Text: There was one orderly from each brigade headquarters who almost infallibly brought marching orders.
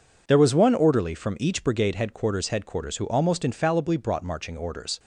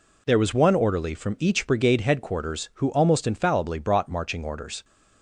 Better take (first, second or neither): second